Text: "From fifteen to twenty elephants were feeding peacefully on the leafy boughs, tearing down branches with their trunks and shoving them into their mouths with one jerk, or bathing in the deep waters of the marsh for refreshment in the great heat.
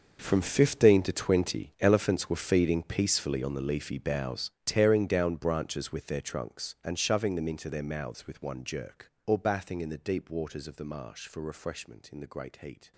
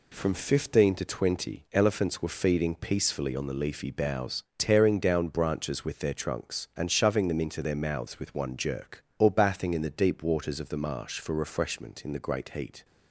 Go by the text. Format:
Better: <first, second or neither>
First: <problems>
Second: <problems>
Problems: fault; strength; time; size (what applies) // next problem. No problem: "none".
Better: second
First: gets quieter; strong; throughout; 16.5 dB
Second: none